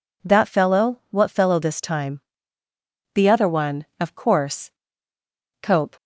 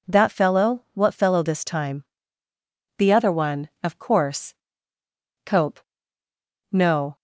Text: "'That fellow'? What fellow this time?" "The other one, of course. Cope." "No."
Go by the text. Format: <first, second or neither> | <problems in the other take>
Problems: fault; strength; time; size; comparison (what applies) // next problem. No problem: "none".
second | stops before "No"; at 5.9 s